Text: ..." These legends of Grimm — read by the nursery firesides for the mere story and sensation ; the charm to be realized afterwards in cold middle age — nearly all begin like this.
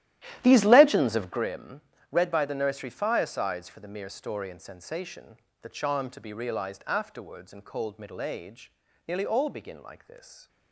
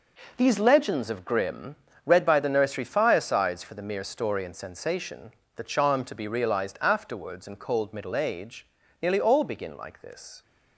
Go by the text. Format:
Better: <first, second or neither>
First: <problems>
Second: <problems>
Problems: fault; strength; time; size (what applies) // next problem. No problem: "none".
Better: second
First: starts louder than the rest; strong; until 1.4 s; 13.5 dB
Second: none